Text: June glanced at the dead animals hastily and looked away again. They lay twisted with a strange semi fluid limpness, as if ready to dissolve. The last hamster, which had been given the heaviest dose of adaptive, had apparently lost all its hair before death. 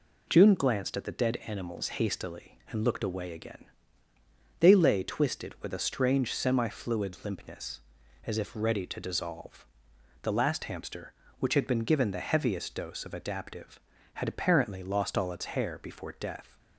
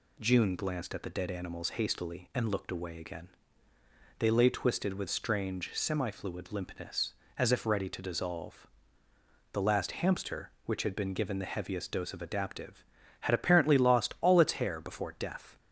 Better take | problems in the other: first | skips "a"; at 5.0 s

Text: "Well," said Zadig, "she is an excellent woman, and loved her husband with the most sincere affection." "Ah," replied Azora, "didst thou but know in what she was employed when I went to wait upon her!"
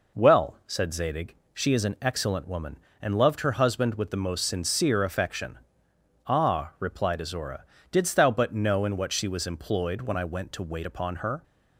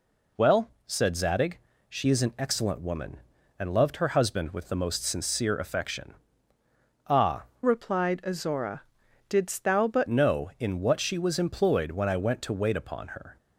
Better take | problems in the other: first | changes voice from "replied" to "but"; from 7.6 to 10.0 s; 2.4 s long

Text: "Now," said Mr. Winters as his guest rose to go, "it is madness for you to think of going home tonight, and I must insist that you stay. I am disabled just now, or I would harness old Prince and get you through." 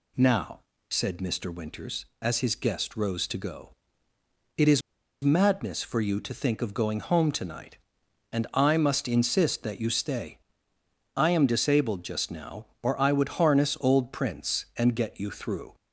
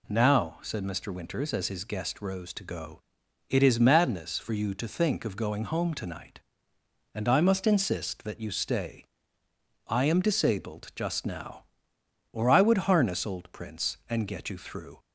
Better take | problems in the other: second | pauses between "is" and "madness"; at 4.8 s; 0.43 s long

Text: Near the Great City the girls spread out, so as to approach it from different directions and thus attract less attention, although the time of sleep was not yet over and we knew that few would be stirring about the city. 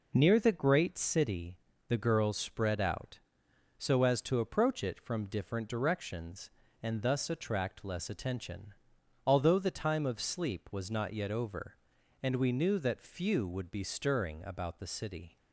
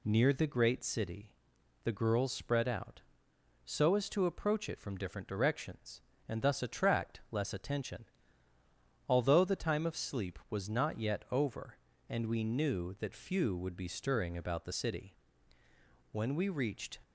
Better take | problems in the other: first | pauses between "City" and "the"; noticeable; at 1.3 s; 0.48 s long; slight in the first // goes on to say "When we reached"; noticeable; from 16.1 s on; 0.88 s long

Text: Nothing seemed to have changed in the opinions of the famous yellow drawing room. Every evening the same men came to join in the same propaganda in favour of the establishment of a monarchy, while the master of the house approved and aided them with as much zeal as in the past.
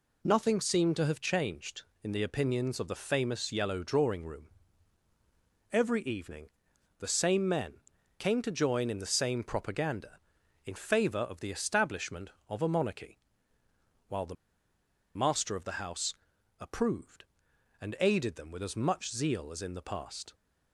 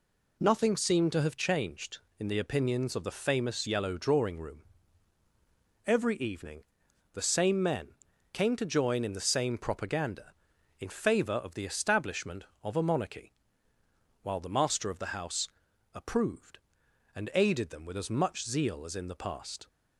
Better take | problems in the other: second | pauses between "evening" and "the"; noticeable; at 6.4 s; 0.50 s long; noticeable in the second // pauses between "men" and "came"; at 7.7 s; 0.40 s long; also in the second // pauses between "the" and "master"; noticeable; at 14.3 s; 0.80 s long // pauses between "house" and "approved"; noticeable; at 16.1 s; 0.46 s long; noticeable in the second

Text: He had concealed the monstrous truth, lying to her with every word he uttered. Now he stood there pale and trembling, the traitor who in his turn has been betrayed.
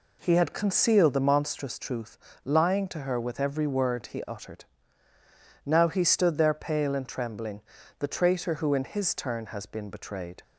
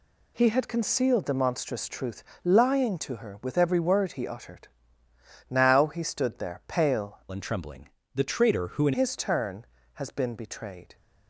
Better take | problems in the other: first | changes voice from "and" to "in"; from 7.2 to 8.9 s; 1.7 s long

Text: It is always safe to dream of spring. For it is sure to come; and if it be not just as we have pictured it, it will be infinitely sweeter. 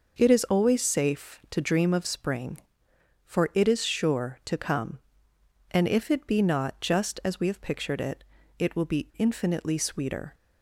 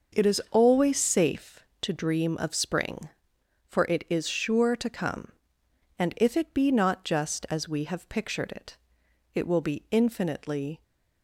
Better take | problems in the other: first | starts louder than the rest; noticeable; until 1.2 s; 6 dB // stops before "sweeter"; at 10.8 s

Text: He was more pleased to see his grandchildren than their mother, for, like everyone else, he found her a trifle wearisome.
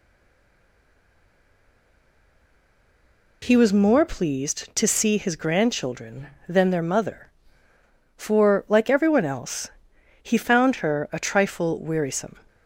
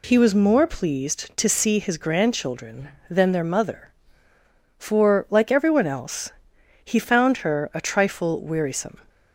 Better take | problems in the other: second | stays silent before the first word; strong; until 3.4 s; 3.4 s long

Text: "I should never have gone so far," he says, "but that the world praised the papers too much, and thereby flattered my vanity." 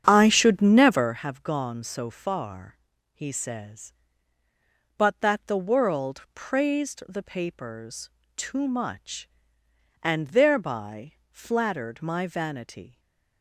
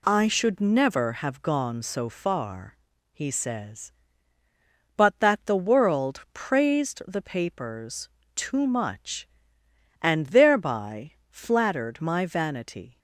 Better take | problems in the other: second | starts louder than the rest; strong; until 1.2 s; 8 dB // pauses between "papers" and "too"; slight; at 8.1 s; 0.24 s long; slight in the second // pauses between "thereby" and "flattered"; slight; at 11.1 s; 0.18 s long; slight in the second // stays silent after the last word; slight; from 12.9 s on; 0.5 s long

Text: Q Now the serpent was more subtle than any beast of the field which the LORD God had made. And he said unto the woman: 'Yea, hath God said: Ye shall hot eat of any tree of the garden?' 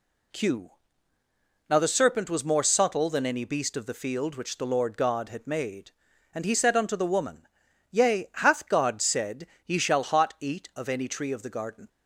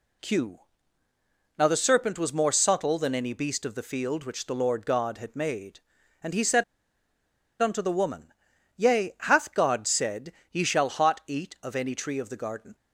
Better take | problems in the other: first | pauses between "Q" and "Now"; noticeable; at 0.5 s; 0.98 s long; noticeable in the first // pauses between "said" and "unto"; at 6.6 s; 0.98 s long

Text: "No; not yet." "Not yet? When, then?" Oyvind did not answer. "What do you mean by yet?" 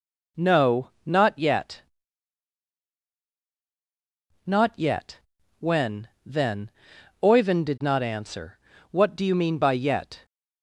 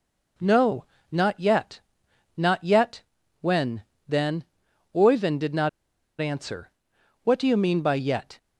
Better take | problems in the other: first | pauses between "not" and "answer"; noticeable; at 5.6 s; 0.51 s long

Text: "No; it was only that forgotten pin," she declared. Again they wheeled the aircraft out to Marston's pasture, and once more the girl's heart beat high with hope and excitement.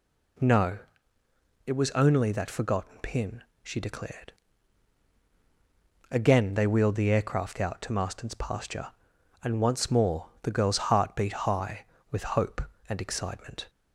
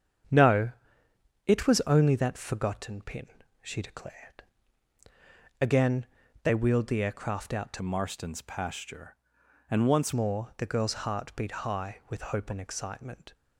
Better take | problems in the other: first | starts louder than the rest; strong; until 2.0 s; 8 dB // pauses between "Again" and "they"; slight; at 6.0 s; 0.34 s long // changes voice from "Marston's" to "once"; from 7.8 to 10.1 s; 2.3 s long

